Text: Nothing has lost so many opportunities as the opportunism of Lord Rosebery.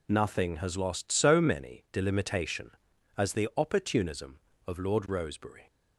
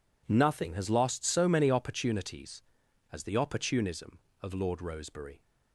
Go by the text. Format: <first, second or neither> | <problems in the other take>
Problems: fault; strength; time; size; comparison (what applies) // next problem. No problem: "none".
second | says "delimitation" for "opportunities"; at 1.9 s